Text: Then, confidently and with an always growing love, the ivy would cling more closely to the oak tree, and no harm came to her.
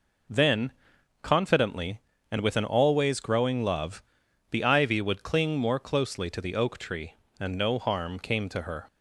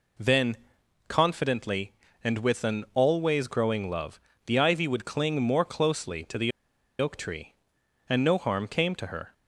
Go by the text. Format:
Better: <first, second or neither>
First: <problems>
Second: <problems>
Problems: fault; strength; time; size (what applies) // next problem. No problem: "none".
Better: first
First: none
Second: pauses between "the" and "oak"; noticeable; at 6.5 s; 0.50 s long